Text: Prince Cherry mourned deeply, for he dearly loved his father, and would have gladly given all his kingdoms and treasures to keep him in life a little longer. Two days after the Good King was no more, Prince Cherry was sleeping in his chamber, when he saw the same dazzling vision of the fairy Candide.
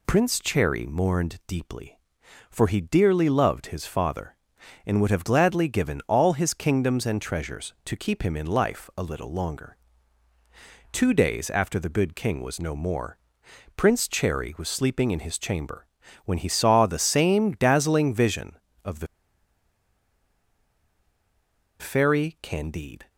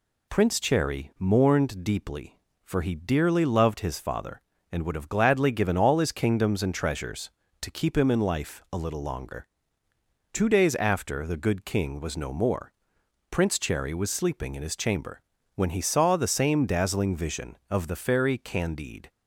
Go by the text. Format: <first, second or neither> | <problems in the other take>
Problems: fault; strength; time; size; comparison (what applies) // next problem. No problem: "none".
second | pauses between "the" and "fairy"; strong; at 19.0 s; 2.7 s long